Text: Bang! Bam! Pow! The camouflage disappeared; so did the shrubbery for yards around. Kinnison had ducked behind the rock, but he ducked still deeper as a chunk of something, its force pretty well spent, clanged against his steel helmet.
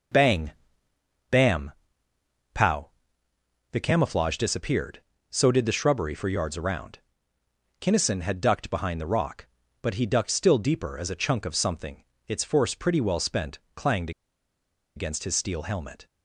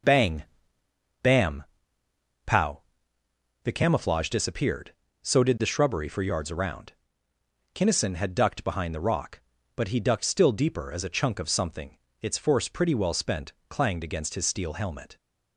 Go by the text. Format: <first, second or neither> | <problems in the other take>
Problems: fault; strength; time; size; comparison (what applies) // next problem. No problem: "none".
second | starts louder than the rest; noticeable; until 2.7 s; 6 dB; noticeable in the second // pauses between "clanged" and "against"; noticeable; at 14.1 s; 0.85 s long